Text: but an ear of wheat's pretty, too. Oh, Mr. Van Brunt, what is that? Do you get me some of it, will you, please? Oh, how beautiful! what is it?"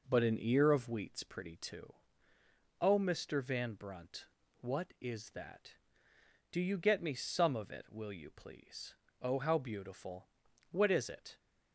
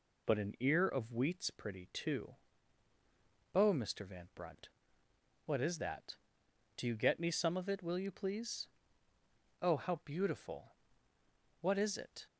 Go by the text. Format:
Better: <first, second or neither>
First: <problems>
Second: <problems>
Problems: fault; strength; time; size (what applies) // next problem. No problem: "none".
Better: neither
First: none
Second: none